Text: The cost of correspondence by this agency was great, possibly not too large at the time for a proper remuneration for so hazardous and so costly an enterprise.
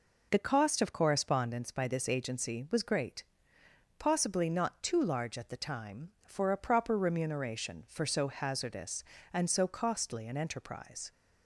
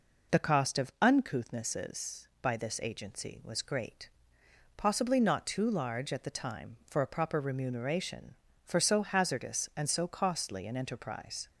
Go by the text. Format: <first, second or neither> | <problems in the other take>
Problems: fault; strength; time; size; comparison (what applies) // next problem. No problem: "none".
first | says "uncouthnesses" for "correspondence"; at 1.0 s